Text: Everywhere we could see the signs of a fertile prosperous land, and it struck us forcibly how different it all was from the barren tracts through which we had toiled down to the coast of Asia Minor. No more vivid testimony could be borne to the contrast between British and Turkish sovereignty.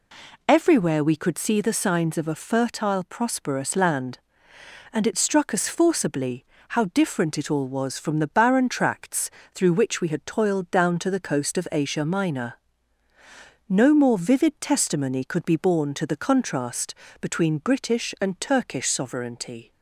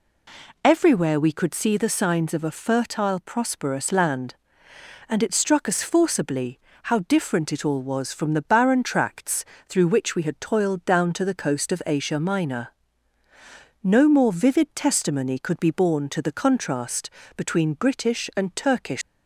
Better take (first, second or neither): first